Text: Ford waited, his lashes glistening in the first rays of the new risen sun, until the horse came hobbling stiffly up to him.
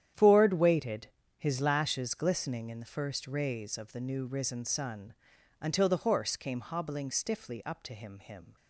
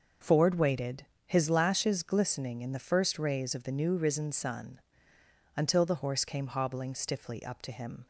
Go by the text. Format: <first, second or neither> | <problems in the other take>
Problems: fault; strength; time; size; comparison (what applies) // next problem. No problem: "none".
second | starts louder than the rest; strong; until 1.4 s; 10 dB; also in the second // says "him" twice; at 8.1 s